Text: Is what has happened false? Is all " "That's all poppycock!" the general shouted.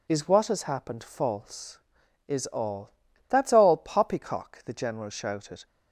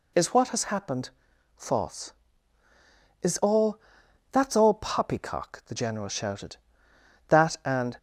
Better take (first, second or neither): first